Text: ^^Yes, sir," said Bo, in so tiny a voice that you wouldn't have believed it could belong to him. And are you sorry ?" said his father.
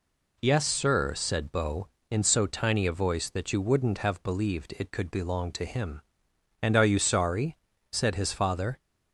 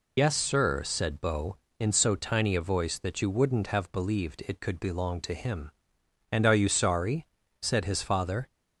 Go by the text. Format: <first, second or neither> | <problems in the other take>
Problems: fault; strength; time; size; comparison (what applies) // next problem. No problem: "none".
first | loses the start of "Yes"; at 0.1 s; 70 ms